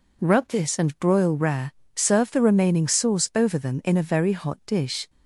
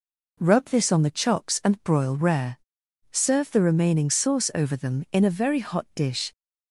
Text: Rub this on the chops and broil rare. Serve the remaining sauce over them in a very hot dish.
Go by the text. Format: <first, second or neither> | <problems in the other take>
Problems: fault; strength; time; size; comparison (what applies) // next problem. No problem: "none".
second | skips "on the chops"; at 0.7 s